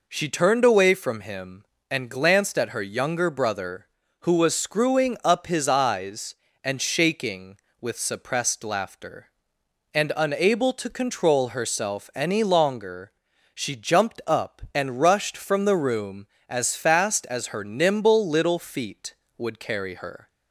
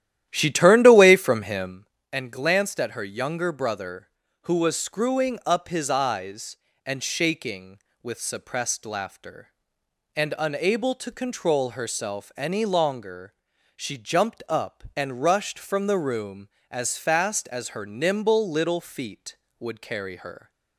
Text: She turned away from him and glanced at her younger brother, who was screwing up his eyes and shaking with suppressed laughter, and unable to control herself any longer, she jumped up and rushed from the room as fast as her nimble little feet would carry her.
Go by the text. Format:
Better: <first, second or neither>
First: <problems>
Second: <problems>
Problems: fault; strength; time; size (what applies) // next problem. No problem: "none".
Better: first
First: none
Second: starts louder than the rest; strong; until 1.8 s; 12 dB